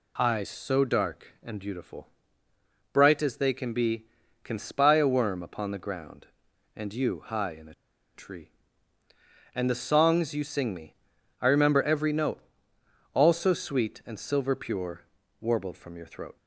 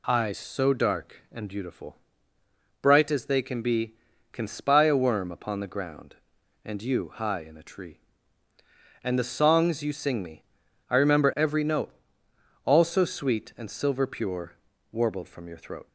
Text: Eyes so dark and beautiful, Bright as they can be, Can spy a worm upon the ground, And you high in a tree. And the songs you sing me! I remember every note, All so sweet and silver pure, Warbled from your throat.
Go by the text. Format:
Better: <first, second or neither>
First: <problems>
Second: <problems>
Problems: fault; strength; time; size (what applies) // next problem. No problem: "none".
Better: second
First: pauses between "a" and "tree"; at 7.7 s; 0.40 s long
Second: none